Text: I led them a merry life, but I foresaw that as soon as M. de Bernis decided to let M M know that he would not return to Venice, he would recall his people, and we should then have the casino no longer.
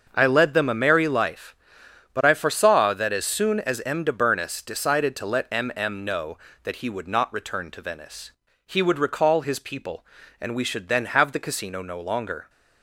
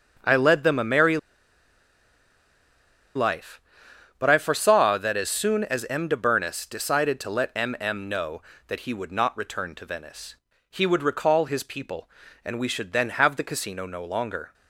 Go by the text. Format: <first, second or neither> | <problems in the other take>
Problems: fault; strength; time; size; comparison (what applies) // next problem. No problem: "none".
first | starts louder than the rest; until 3.2 s; 6.5 dB; also in the first // pauses between "merry" and "life"; strong; at 1.1 s; 1.9 s long